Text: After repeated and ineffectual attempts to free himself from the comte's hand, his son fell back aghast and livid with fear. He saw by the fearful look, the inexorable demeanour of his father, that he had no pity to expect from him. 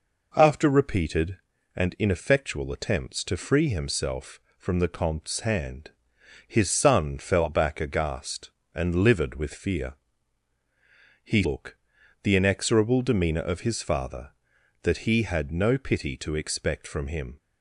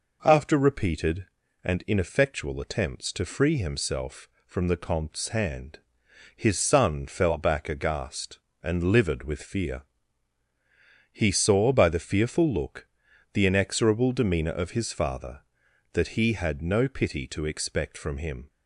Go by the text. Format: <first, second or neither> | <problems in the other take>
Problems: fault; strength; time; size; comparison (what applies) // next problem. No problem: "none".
second | skips "saw by the fearful"; at 11.4 s